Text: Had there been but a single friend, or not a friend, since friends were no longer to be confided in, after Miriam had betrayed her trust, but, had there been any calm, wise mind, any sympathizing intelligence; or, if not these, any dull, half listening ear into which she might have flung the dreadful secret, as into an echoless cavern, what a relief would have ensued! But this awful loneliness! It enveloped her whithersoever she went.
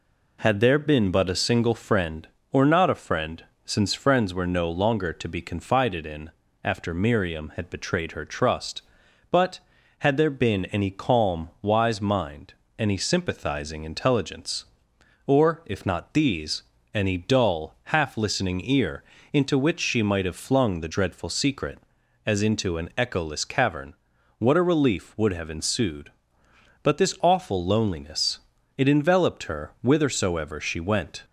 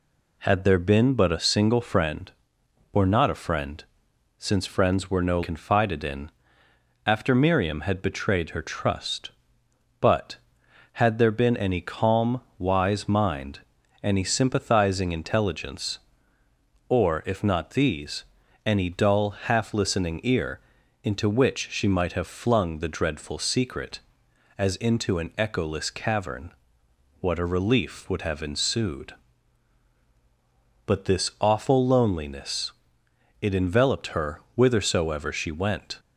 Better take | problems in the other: first | skips "longer to be"; at 5.4 s // pauses between "ear" and "into"; at 20.5 s; 0.42 s long; slight in the first

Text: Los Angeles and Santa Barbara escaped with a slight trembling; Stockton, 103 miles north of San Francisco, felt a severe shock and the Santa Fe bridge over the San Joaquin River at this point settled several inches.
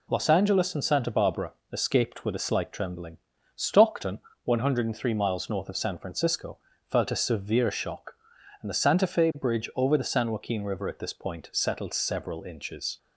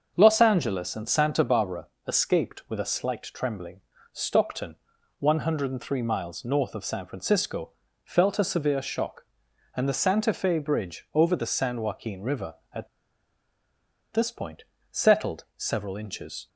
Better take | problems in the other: first | starts louder than the rest; until 1.1 s; 6.5 dB // pauses between "Barbara" and "escaped"; slight; at 1.8 s; 0.18 s long; slight in the first // pauses between "at" and "this"; strong; at 12.8 s; 1.2 s long // pauses between "point" and "settled"; slight; at 14.6 s; 0.26 s long

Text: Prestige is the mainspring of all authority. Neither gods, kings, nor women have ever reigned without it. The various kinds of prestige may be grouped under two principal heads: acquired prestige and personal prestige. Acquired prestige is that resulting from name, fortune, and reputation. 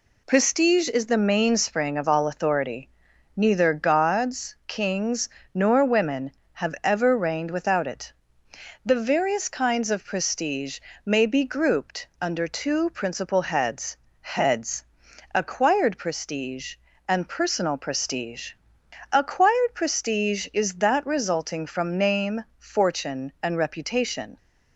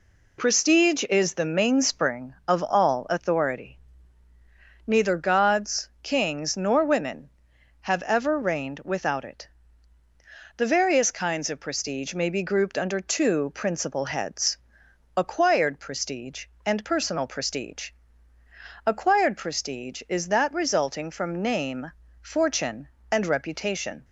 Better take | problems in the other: second | pauses between "prestige" and "may"; slight; at 10.7 s; 0.26 s long // says "heads" twice; at 14.2 s

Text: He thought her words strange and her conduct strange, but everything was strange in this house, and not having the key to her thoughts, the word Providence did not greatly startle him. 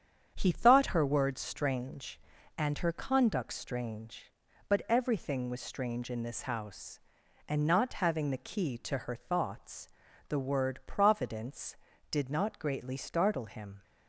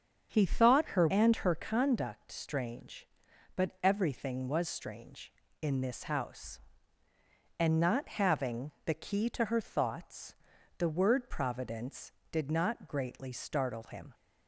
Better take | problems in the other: first | starts louder than the rest; strong; until 1.3 s; 7.5 dB; strong in the first // skips "words strange"; at 1.0 s // pauses between "having" and "the"; slight; at 8.6 s; 0.16 s long

